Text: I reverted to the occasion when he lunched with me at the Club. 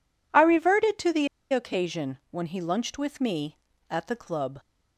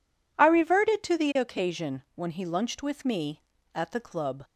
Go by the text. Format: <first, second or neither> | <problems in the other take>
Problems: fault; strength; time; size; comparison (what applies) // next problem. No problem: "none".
second | pauses between "the" and "occasion"; slight; at 1.2 s; 0.26 s long